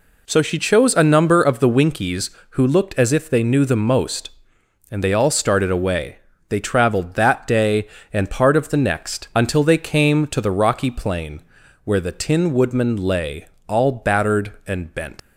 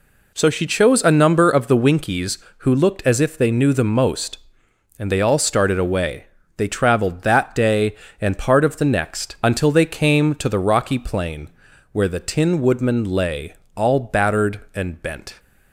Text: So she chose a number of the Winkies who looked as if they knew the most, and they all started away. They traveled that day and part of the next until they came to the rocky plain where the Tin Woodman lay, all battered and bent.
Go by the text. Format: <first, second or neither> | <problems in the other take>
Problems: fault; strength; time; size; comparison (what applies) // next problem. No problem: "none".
second | pauses between "plain" and "where"; at 11.4 s; 0.44 s long; also in the second // leaves "bent" unfinished; at 15.1 s; 115 ms